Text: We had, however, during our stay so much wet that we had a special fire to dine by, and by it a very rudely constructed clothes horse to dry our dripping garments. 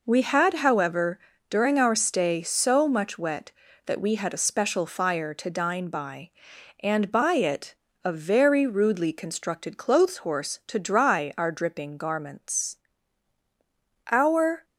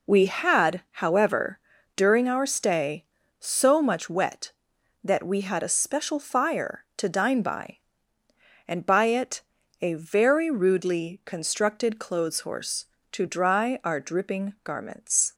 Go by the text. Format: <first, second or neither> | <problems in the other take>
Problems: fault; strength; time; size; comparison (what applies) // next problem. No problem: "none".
second | pauses between "it" and "a"; slight; at 7.7 s; 0.30 s long; also in the second // goes on to say "Our"; from 14.1 s on; 0.54 s long